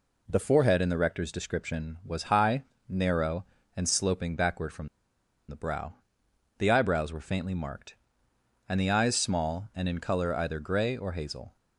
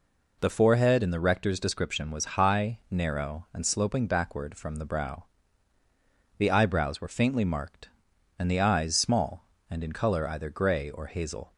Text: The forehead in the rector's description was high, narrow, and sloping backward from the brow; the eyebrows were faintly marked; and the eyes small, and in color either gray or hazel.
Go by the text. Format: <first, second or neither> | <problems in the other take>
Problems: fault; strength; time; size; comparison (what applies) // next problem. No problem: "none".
second | pauses between "from" and "the"; noticeable; at 4.8 s; 0.61 s long